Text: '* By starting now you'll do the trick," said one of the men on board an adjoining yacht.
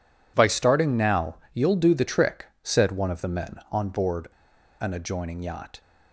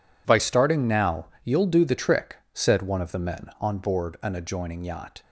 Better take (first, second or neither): second